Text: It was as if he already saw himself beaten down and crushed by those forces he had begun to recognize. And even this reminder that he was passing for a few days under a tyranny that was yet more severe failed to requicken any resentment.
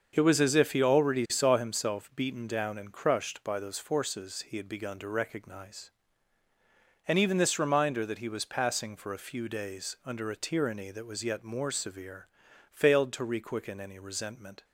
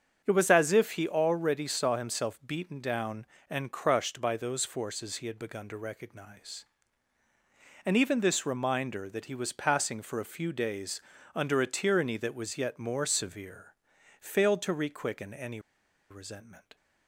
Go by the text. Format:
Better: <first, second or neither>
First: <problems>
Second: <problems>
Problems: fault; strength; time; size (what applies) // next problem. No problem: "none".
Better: first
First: starts louder than the rest; until 1.1 s; 6.5 dB // pauses between "severe" and "failed"; noticeable; at 12.2 s; 0.46 s long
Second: starts louder than the rest; until 1.2 s; 7 dB // pauses between "days" and "under"; slight; at 11.0 s; 0.34 s long // pauses between "severe" and "failed"; noticeable; at 13.7 s; 0.46 s long // pauses between "any" and "resentment"; noticeable; at 15.5 s; 0.51 s long